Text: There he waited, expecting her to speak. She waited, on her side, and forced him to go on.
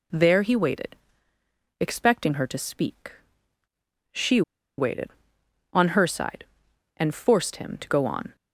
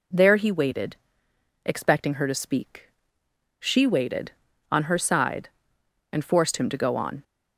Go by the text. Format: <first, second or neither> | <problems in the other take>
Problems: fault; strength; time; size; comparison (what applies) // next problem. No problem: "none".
second | pauses between "She" and "waited"; at 4.4 s; 0.36 s long